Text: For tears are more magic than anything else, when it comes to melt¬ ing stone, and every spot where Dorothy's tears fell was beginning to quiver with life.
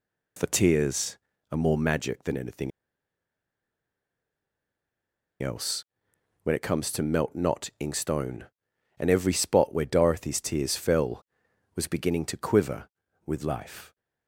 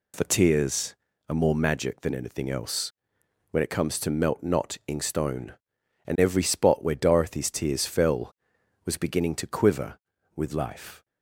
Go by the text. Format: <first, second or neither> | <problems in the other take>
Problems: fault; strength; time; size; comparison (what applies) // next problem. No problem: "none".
second | pauses between "anything" and "else"; strong; at 2.7 s; 2.7 s long